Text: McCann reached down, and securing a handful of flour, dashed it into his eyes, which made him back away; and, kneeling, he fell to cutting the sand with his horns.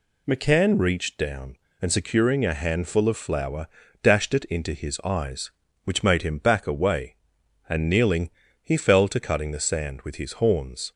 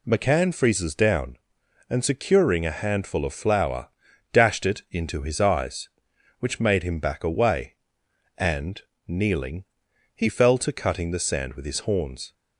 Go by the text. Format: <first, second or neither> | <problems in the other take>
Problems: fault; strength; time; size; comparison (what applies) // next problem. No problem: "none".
first | says "freezes" for "reached"; at 0.5 s